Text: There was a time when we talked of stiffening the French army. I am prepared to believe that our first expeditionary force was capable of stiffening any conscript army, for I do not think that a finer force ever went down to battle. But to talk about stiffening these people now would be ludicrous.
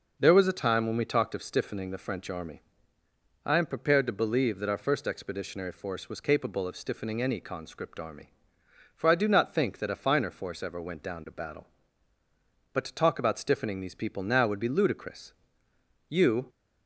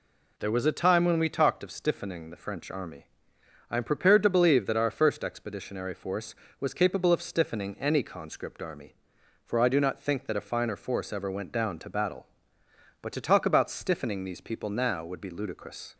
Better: second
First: goes on to say "You"; slight; from 16.0 s on; 0.40 s long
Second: none

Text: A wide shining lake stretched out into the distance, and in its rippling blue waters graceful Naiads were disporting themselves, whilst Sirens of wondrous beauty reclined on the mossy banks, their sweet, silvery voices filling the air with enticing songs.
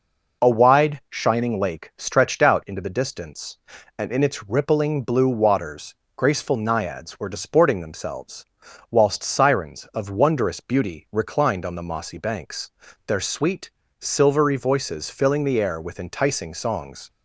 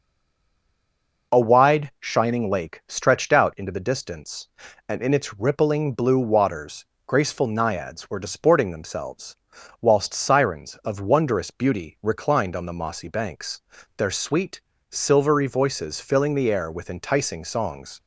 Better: first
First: pauses between "waters" and "graceful"; slight; at 5.9 s; 0.22 s long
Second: stays silent before the first word; noticeable; until 1.3 s; 1.3 s long // pauses between "waters" and "graceful"; slight; at 6.8 s; 0.22 s long

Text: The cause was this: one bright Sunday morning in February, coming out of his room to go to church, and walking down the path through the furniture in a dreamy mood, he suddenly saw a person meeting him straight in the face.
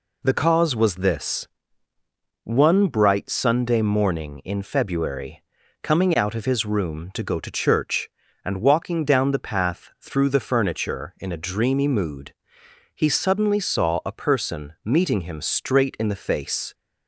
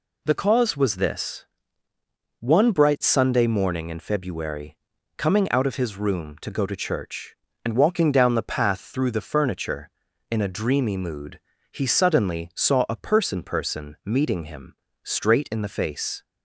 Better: first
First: none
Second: says "person" twice; at 13.4 s // pauses between "him" and "straight"; slight; at 14.7 s; 0.30 s long

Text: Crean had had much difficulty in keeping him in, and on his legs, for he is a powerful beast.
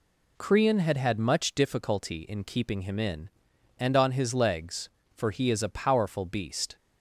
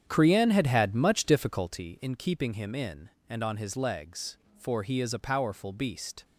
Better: first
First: none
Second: starts louder than the rest; strong; until 1.9 s; 8.5 dB

